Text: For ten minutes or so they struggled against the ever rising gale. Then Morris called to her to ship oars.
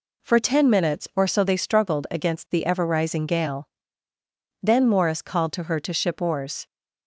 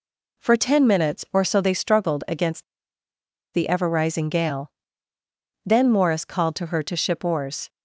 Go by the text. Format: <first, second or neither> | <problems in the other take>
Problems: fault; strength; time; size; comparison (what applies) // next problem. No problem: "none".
first | pauses between "against" and "the"; noticeable; at 2.6 s; 0.90 s long